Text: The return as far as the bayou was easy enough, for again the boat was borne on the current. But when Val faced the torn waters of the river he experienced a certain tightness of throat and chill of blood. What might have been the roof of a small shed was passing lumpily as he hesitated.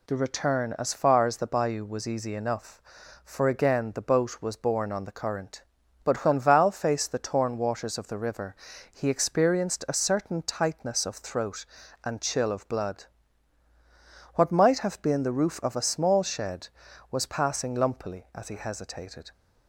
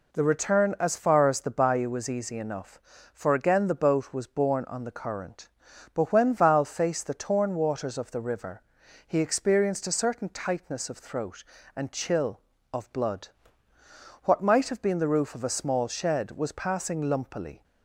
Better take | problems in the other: first | pauses between "river" and "he"; noticeable; at 8.6 s; 0.46 s long; slight in the first // stops before "as he hesitated"; at 17.6 s

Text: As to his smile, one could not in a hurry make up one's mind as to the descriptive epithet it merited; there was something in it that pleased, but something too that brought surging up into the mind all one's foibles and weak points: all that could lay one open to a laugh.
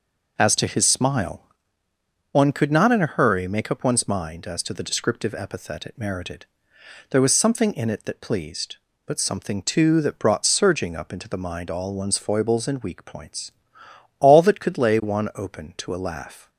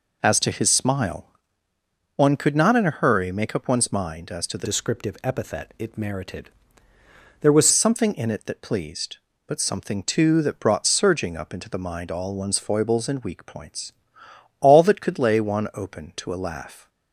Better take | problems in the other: first | changes voice from "descriptive" to "was"; from 4.6 to 7.6 s; 3.0 s long

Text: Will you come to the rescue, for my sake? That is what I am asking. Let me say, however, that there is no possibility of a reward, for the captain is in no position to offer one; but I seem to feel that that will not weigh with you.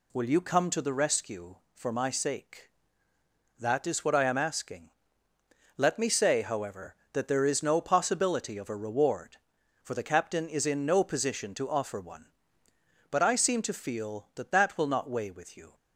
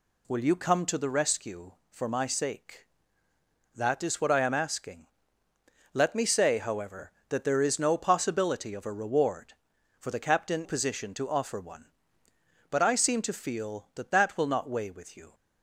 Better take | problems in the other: first | skips "is in no"; at 10.6 s

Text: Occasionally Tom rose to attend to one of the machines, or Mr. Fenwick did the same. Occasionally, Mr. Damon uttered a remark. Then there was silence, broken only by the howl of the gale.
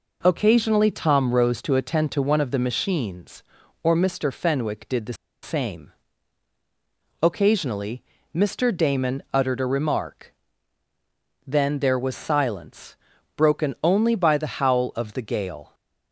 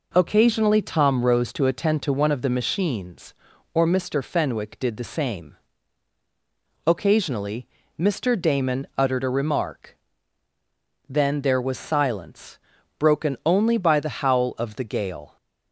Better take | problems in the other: second | pauses between "the" and "same"; slight; at 5.1 s; 0.29 s long

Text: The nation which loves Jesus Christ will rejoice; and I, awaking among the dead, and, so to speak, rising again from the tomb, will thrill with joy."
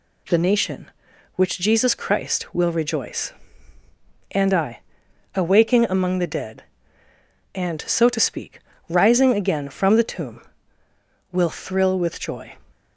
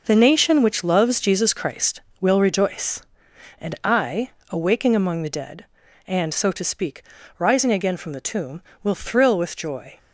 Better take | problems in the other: second | skips "loves"; at 1.5 s

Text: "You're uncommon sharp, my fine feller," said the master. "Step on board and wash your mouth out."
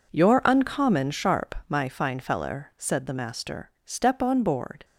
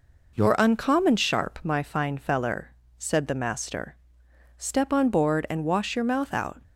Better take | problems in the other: second | stops before "and wash your mouth out"; at 4.8 s

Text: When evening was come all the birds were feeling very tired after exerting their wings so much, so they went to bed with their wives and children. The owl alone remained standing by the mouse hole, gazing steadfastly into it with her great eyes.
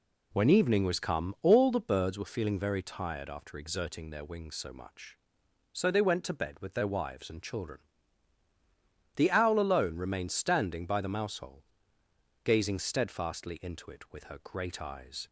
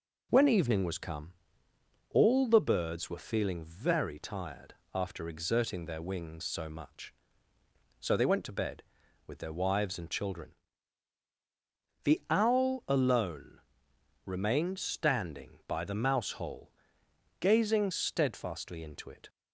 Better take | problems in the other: first | pauses between "come" and "all"; noticeable; at 1.3 s; 0.80 s long // pauses between "tired" and "after"; slight; at 4.7 s; 0.20 s long // pauses between "alone" and "remained"; noticeable; at 13.5 s; 0.66 s long // stops before "with her great eyes"; at 19.2 s

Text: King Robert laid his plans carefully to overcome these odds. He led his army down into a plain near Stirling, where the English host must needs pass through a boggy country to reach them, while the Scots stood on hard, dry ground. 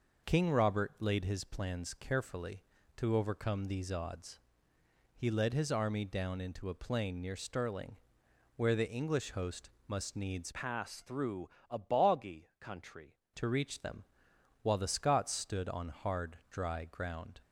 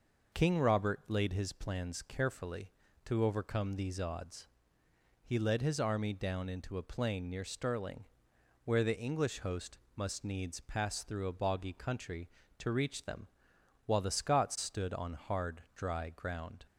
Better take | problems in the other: second | pauses between "host" and "must"; slight; at 9.6 s; 0.16 s long; slight in the second // changes voice from "pass" to "country"; from 10.5 to 13.1 s; 2.6 s long // pauses between "through" and "a"; slight; at 11.4 s; 0.22 s long

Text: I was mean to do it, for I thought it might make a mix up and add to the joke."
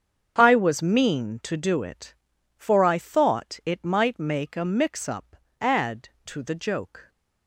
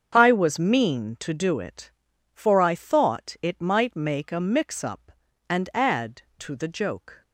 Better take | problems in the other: second | starts louder than the rest; strong; until 1.3 s; 7 dB; also in the second // skips "and"; at 5.4 s

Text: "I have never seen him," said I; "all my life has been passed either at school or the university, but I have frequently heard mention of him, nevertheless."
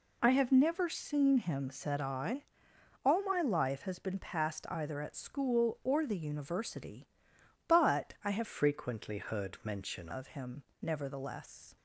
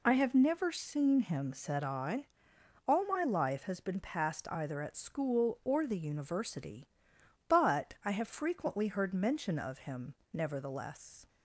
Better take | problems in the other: second | changes voice from "frequently" to "mention"; from 8.4 to 10.0 s; 1.6 s long

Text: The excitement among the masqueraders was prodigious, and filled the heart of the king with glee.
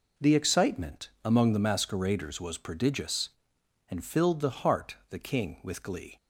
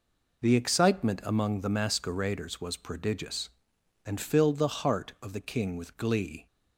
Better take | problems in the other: second | skips "of"; at 5.0 s

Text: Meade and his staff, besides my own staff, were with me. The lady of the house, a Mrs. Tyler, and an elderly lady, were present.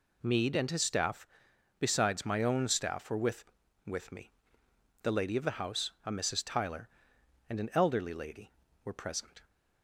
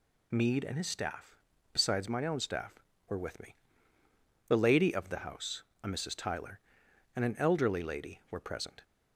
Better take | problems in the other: second | says "with" twice; at 3.8 s

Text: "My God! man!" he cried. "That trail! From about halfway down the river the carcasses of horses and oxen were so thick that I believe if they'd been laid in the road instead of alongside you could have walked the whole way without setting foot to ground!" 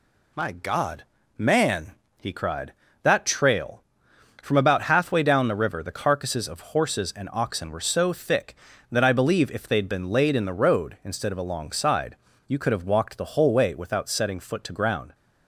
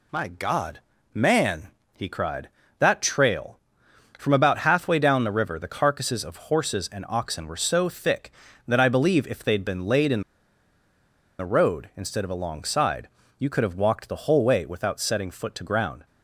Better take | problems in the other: first | pauses between "in" and "the"; at 10.2 s; 1.1 s long // pauses between "alongside" and "you"; slight; at 13.0 s; 0.30 s long; slight in the first

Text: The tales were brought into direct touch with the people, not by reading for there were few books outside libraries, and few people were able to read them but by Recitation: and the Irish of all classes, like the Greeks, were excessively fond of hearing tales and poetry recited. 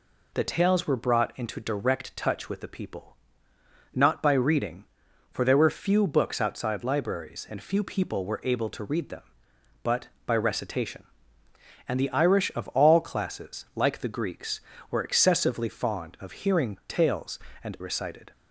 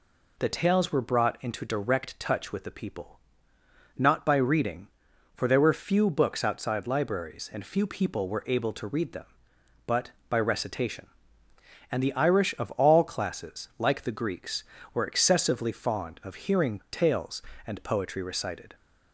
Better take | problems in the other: second | skips "poetry"; at 17.7 s

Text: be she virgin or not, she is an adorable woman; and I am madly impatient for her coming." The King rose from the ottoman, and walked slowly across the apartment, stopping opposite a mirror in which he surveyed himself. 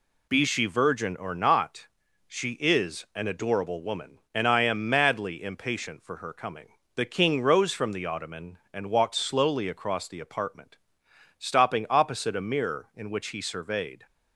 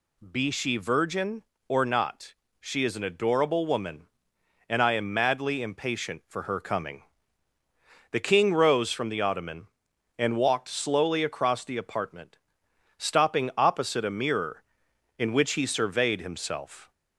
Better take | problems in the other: second | stops before "himself"; at 14.0 s

